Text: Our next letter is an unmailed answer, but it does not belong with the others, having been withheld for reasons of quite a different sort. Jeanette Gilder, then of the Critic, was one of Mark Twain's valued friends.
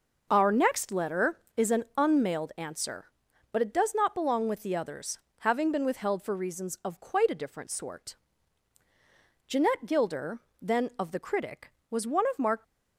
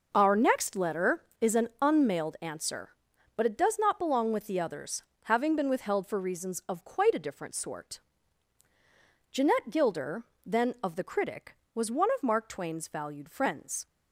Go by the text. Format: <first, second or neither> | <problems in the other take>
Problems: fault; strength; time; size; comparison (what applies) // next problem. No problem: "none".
second | stops before "Twain's valued friends"; at 12.6 s